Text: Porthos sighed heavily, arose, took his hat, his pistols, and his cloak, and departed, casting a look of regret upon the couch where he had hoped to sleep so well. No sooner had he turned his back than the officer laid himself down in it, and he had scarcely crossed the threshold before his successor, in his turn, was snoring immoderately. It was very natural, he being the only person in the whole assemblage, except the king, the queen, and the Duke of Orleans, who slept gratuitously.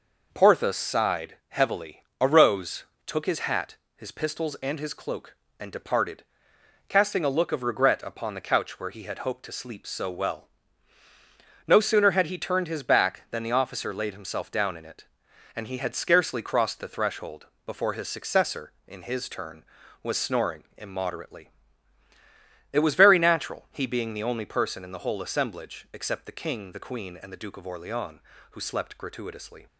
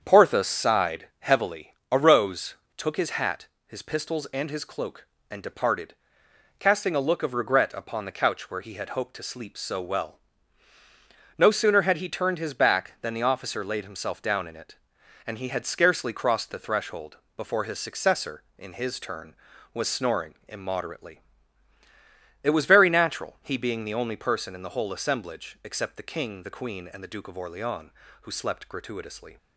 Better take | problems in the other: first | starts louder than the rest; strong; until 1.5 s; 7.5 dB // pauses between "threshold" and "before"; slight; at 17.1 s; 0.20 s long; slight in the first

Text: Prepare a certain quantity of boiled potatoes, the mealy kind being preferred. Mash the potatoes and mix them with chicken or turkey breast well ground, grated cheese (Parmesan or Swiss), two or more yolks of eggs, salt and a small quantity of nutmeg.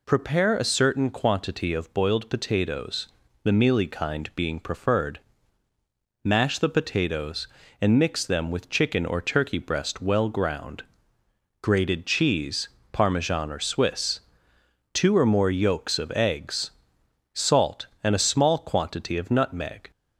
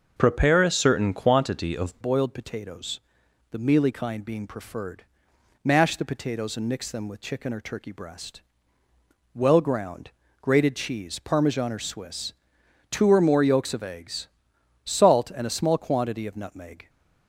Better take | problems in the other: first | starts louder than the rest; noticeable; until 1.1 s; 6 dB // changes voice at "boiled"; from 2.0 s on; 14.8 s long // pauses between "breast" and "well"; noticeable; at 8.4 s; 0.94 s long

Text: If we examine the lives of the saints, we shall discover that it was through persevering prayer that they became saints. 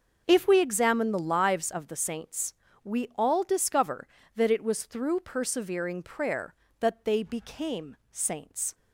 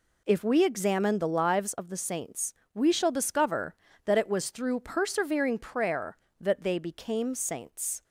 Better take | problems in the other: second | starts louder than the rest; noticeable; until 1.2 s; 6 dB // says "all" for "shall"; at 3.1 s

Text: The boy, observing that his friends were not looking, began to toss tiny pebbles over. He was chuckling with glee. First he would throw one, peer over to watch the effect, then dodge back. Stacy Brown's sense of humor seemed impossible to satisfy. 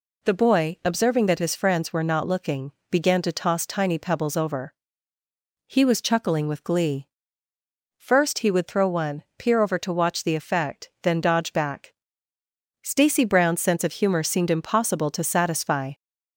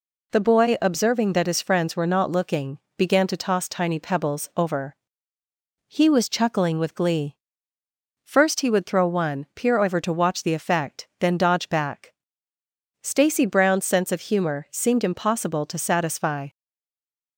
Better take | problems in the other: first | stays silent after the last word; slight; from 16.4 s on; 0.9 s long

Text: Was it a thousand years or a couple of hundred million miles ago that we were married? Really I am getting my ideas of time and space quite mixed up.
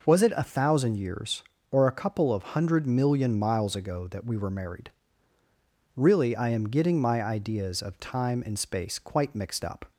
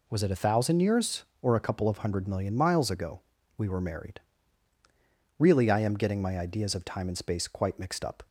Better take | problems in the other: first | skips "that"; at 3.3 s

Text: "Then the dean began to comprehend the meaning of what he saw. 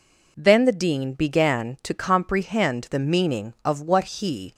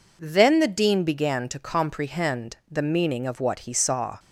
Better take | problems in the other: second | stops before "saw"; at 4.5 s

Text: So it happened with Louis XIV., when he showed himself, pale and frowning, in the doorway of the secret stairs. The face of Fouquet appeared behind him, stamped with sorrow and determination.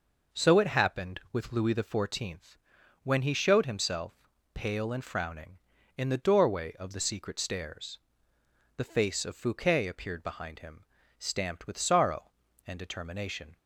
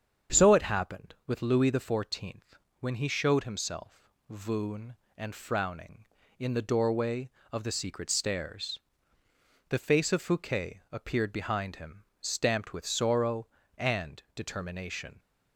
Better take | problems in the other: first | starts louder than the rest; strong; until 1.4 s; 7.5 dB // says "voon" for "pale"; at 4.2 s

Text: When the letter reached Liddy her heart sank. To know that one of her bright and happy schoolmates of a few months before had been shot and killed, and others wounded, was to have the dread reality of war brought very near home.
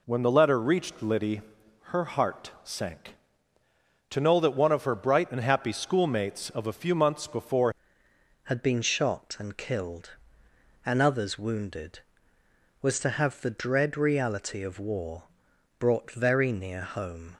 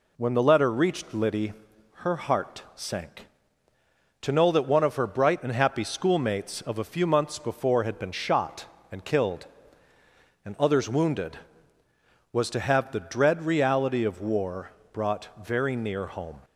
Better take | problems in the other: second | pauses between "Liddy" and "her"; noticeable; at 1.4 s; 0.46 s long; noticeable in the second // changes voice at "had"; from 8.4 s on; 8.9 s long // pauses between "war" and "brought"; noticeable; at 15.2 s; 0.56 s long; slight in the second

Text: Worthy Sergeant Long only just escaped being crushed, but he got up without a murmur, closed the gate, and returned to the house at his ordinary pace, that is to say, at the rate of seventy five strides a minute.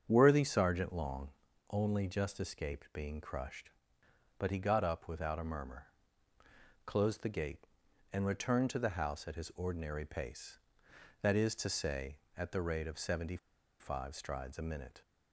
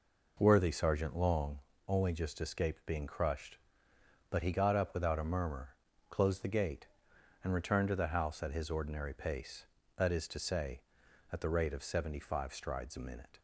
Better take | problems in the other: second | starts louder than the rest; strong; until 1.0 s; 7.5 dB // pauses between "Long" and "only"; at 1.3 s; 0.40 s long; slight in the second // pauses between "seventy" and "five"; at 13.3 s; 0.43 s long

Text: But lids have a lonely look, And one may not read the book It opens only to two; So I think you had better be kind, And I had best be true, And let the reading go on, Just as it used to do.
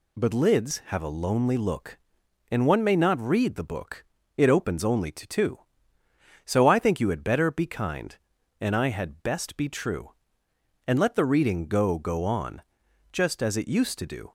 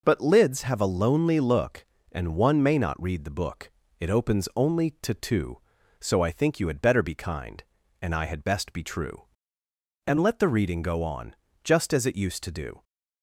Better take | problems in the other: second | pauses between "book" and "It"; slight; at 4.0 s; 0.34 s long; slight in the second // says "go" twice; at 11.9 s

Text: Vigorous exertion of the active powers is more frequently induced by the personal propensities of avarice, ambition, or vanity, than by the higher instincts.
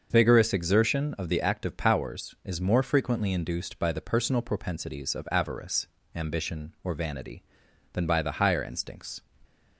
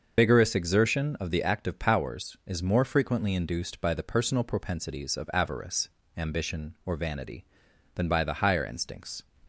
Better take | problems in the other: first | loses the start of "Vigorous"; at 0.1 s; 60 ms // starts louder than the rest; until 1.2 s; 6.5 dB; also in the first

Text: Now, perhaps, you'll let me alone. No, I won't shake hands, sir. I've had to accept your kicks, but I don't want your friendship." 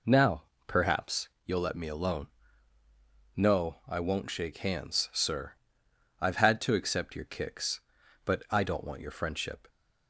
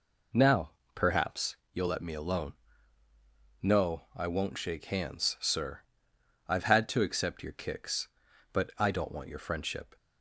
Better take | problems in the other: neither | none

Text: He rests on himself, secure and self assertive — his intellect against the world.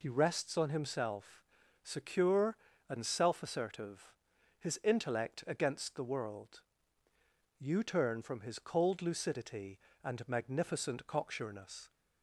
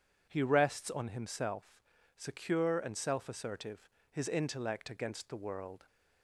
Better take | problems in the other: second | goes on to say "You turn from his cold lucidity and magnificent cocksureness"; strong; from 7.5 s on; 4.3 s long

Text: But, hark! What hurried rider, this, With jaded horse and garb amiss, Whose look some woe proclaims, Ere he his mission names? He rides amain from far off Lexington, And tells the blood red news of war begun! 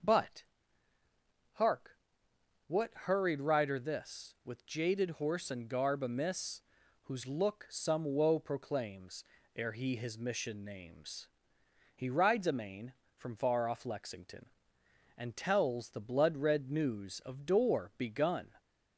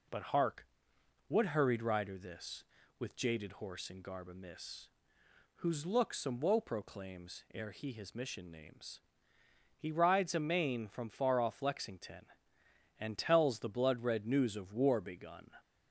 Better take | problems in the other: second | starts louder than the rest; noticeable; until 2.9 s; 6 dB // says "door" for "war"; at 17.4 s

